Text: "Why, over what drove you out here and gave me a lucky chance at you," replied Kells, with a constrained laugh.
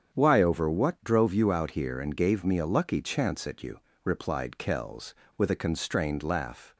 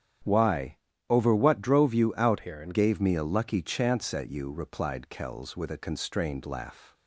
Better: first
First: starts louder than the rest; strong; until 1.1 s; 7.5 dB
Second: starts louder than the rest; strong; until 1.5 s; 9.5 dB // changes voice from "here" to "and"; from 2.3 to 2.7 s; 0.4 s long

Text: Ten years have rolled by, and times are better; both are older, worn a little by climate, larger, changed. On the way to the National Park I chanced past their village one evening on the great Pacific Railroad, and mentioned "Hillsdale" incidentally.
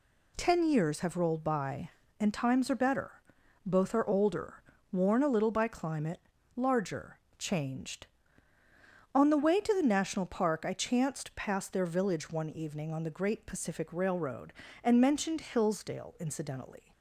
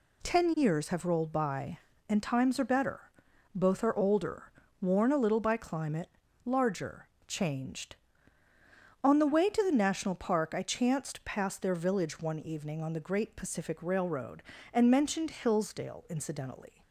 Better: neither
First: none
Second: none

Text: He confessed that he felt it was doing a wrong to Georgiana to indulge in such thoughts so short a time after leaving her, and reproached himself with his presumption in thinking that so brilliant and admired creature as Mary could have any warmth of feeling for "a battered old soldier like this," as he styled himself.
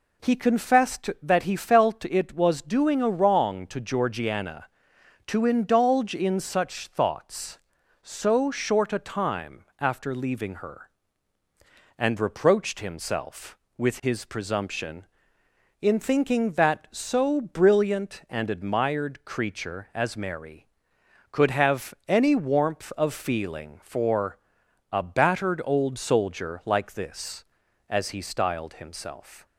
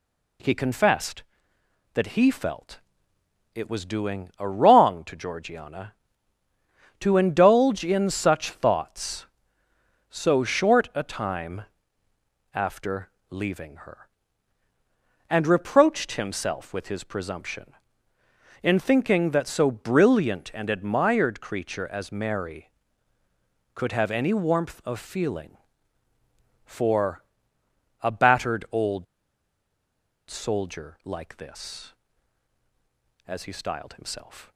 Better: first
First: pauses between "for" and "a"; noticeable; at 24.3 s; 0.54 s long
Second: pauses between "felt" and "it"; noticeable; at 2.7 s; 0.74 s long // pauses between "time" and "after"; noticeable; at 11.6 s; 0.92 s long // pauses between "after" and "leaving"; slight; at 13.0 s; 0.20 s long // pauses between "for" and "a"; noticeable; at 27.2 s; 0.80 s long // pauses between "old" and "soldier"; at 29.0 s; 1.2 s long

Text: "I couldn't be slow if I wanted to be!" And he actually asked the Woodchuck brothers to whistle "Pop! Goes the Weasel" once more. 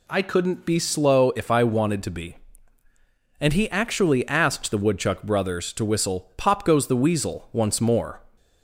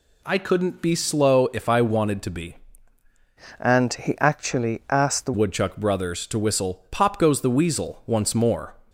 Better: first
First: none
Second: changes voice from "And" to "the"; from 3.5 to 5.3 s; 1.8 s long

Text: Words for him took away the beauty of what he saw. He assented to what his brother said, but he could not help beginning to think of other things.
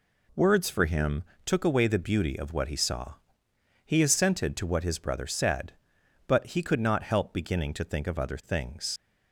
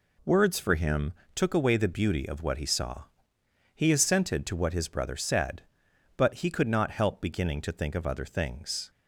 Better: second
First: pauses between "him" and "took"; slight; at 1.2 s; 0.20 s long // leaves "things" unfinished; at 8.9 s; 80 ms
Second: pauses between "him" and "took"; slight; at 1.1 s; 0.20 s long

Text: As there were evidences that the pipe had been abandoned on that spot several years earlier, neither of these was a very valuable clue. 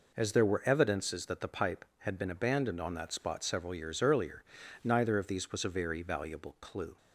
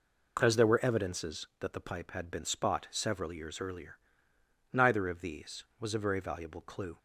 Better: first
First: none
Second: skips "abandoned on that"; at 2.4 s

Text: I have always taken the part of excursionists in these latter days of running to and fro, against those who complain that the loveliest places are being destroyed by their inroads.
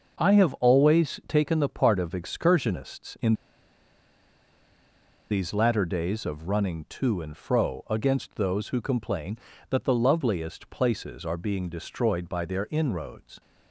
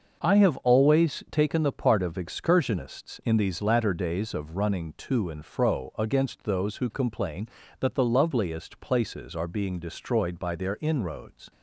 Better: second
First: starts louder than the rest; noticeable; until 1.2 s; 6 dB // pauses between "in" and "these"; strong; at 3.3 s; 1.9 s long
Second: starts louder than the rest; noticeable; until 1.3 s; 6 dB

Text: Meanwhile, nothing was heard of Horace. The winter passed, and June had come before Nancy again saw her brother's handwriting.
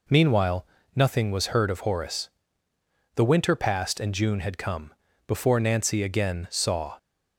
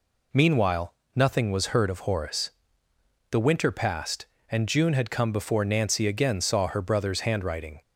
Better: second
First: pauses between "come" and "before"; slight; at 4.9 s; 0.32 s long // stops before "her brother's handwriting"; at 6.9 s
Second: none

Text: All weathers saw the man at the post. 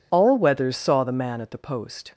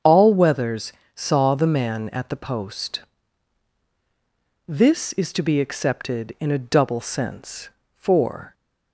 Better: first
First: none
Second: starts louder than the rest; strong; until 1.2 s; 8 dB // pauses between "weathers" and "saw"; slight; at 0.9 s; 0.22 s long // goes on to say "This is to be accepted in a double sense for"; strong; from 4.6 s on; 3.8 s long

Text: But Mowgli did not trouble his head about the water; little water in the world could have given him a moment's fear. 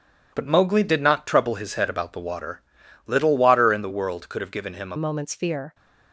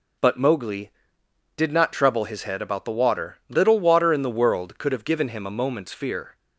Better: second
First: changes voice at "moment's"; from 4.9 s on; 0.8 s long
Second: none

